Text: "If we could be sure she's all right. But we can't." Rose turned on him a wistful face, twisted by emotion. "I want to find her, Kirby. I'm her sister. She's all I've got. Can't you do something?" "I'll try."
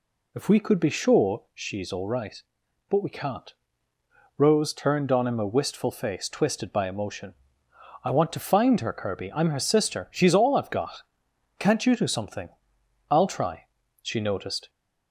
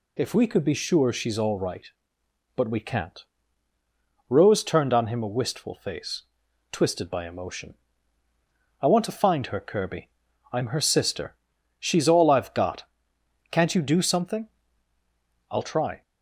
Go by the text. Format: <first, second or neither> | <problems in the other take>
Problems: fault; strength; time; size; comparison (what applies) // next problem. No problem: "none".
second | goes on to say "She noticed"; noticeable; from 14.0 s on; 0.68 s long